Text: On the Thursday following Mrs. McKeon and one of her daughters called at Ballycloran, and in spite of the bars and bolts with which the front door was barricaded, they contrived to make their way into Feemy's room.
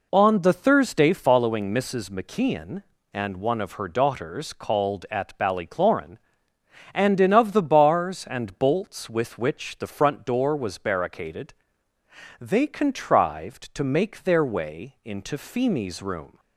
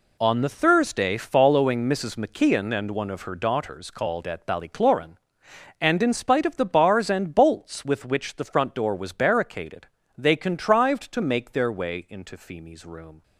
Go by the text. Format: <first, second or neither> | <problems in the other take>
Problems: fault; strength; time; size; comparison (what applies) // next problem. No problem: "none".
second | skips "spite"; at 7.3 s